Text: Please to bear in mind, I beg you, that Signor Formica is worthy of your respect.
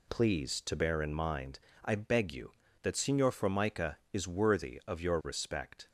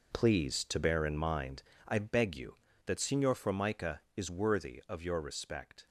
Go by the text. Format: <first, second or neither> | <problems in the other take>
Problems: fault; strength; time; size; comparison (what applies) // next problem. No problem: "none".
first | gets quieter; strong; throughout; 11.5 dB